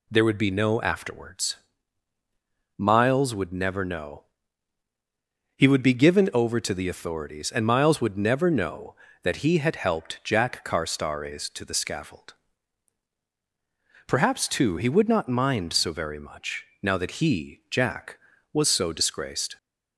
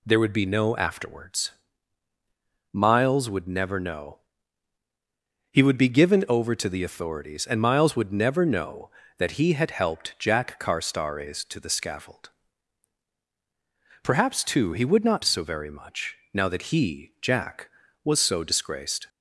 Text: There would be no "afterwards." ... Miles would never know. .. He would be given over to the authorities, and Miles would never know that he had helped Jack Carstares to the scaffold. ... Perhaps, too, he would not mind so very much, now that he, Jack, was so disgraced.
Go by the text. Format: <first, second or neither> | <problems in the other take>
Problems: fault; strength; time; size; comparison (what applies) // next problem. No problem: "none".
first | skips "mind"; at 15.2 s